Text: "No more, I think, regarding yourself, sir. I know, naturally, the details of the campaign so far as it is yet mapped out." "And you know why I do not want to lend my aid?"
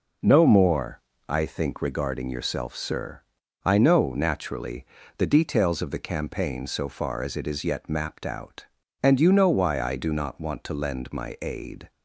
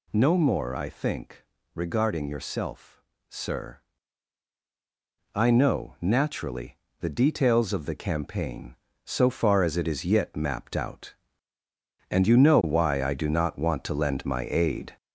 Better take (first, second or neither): first